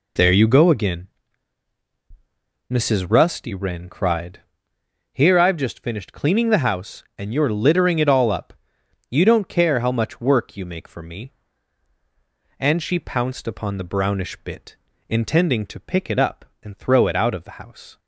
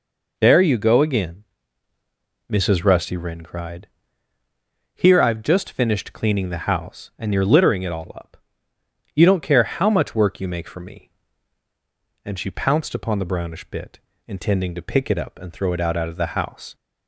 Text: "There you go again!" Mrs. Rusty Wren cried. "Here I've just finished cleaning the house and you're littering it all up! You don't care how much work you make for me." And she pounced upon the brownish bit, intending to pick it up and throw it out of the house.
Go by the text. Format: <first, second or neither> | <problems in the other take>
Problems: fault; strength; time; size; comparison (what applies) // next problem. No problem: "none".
first | says "out" twice; at 15.9 s